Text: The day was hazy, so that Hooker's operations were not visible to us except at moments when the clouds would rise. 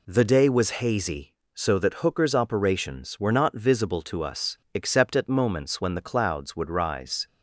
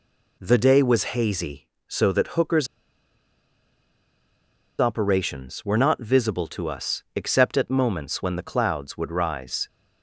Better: first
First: none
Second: pauses between "Hooker's" and "operations"; strong; at 2.6 s; 2.1 s long

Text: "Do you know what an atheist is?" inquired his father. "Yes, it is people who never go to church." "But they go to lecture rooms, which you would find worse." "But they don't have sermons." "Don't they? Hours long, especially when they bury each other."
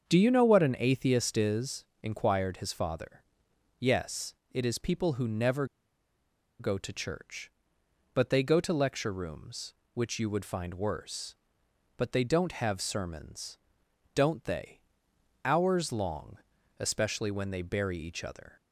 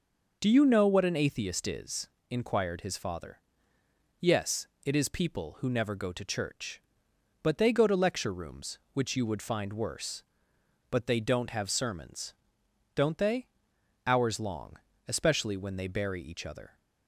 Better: second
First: starts louder than the rest; until 1.1 s; 7 dB // pauses between "never" and "go"; noticeable; at 5.6 s; 0.93 s long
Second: none

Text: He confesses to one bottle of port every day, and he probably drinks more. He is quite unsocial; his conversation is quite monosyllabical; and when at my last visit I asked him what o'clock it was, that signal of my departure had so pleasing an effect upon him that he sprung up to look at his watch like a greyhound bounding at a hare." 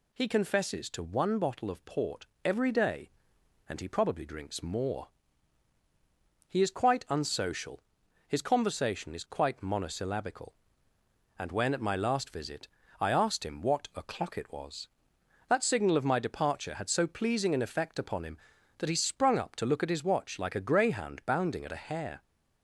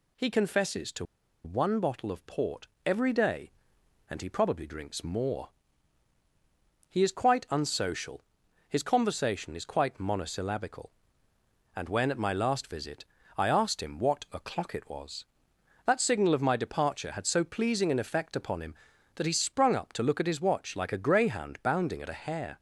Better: first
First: pauses between "port" and "every"; slight; at 2.2 s; 0.18 s long // pauses between "visit" and "I"; slight; at 12.6 s; 0.32 s long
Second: pauses between "to" and "one"; at 1.0 s; 0.40 s long // pauses between "port" and "every"; slight; at 2.6 s; 0.18 s long // pauses between "visit" and "I"; slight; at 13.0 s; 0.32 s long

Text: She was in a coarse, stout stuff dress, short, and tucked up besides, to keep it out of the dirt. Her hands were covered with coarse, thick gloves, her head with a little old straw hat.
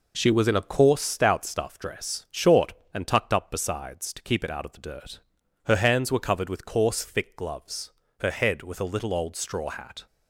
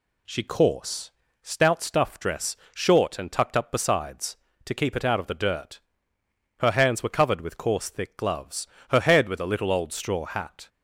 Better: first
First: none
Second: skips "was in a"; at 0.4 s

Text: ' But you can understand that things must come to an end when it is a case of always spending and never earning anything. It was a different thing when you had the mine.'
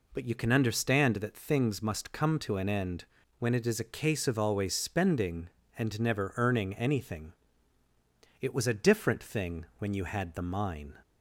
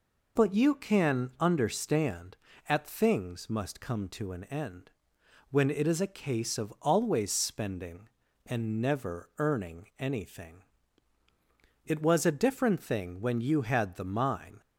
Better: first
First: pauses between "end" and "when"; slight; at 3.0 s; 0.36 s long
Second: says "at" for "that"; at 2.6 s // pauses between "end" and "when"; noticeable; at 4.9 s; 0.58 s long

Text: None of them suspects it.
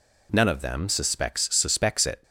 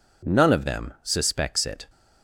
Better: second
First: says "suspects" twice; at 1.5 s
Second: none

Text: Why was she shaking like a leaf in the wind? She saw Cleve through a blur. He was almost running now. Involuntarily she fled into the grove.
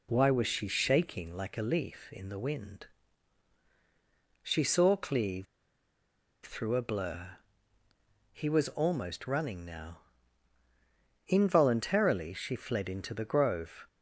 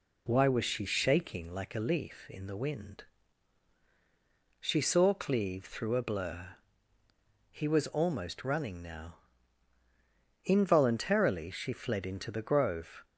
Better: second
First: pauses between "Cleve" and "through"; at 5.4 s; 0.99 s long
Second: none

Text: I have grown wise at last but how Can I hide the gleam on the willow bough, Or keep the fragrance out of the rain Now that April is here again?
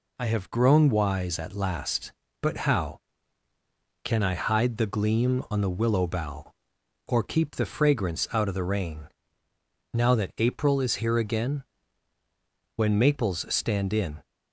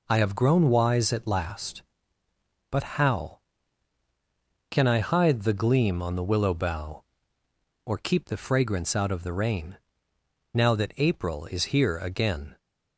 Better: second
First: pauses between "rain" and "Now"; noticeable; at 9.0 s; 0.84 s long // goes on to say "When maples stand in"; from 12.7 s on; 1.4 s long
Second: pauses between "rain" and "Now"; noticeable; at 9.7 s; 0.78 s long

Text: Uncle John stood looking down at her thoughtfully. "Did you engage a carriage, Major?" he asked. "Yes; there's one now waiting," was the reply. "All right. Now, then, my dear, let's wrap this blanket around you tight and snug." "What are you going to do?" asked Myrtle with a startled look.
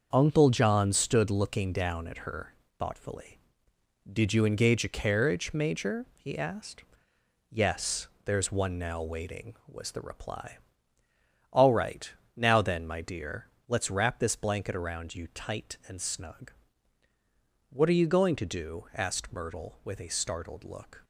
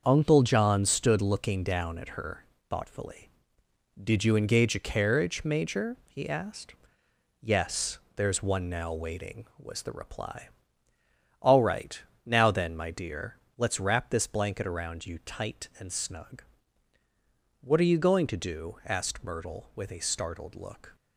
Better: neither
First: starts louder than the rest; until 1.1 s; 6.5 dB // pauses between "her" and "thoughtfully"; slight; at 2.5 s; 0.24 s long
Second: starts louder than the rest; until 1.0 s; 6.5 dB // pauses between "her" and "thoughtfully"; slight; at 2.4 s; 0.24 s long

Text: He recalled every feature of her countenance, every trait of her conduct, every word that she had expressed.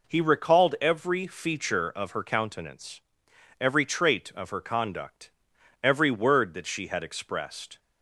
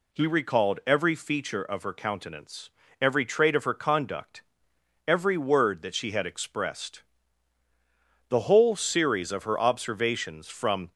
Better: first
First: none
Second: goes on to say "The whole series of her observations from"; strong; from 8.2 s on; 2.6 s long

